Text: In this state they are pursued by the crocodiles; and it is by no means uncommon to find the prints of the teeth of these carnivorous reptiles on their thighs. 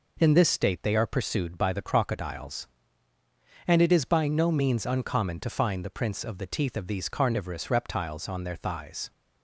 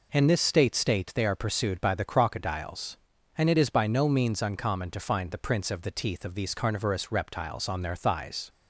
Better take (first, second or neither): first